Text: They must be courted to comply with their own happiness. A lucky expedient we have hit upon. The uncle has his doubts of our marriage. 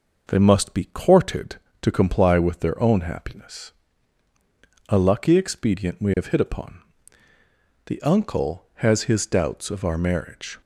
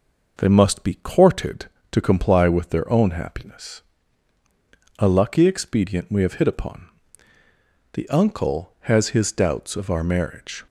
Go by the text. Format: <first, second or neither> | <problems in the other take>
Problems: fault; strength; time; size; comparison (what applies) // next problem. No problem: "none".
neither | none